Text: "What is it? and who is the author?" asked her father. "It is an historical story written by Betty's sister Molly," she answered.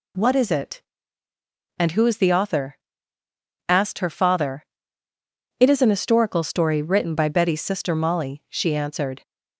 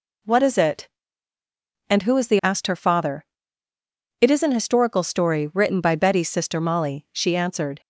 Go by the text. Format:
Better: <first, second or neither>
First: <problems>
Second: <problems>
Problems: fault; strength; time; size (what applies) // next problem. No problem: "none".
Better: first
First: none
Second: skips "author"; at 2.3 s